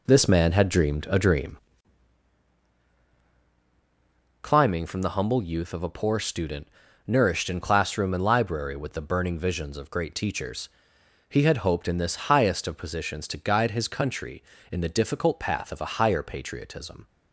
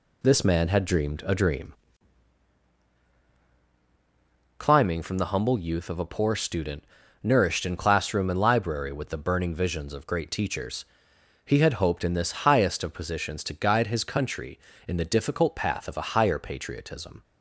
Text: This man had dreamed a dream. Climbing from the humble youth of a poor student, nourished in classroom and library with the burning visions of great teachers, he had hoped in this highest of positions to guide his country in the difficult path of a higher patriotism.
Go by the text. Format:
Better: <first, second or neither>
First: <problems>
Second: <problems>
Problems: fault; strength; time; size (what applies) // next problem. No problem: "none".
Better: second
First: starts louder than the rest; until 1.8 s; 3.5 dB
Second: none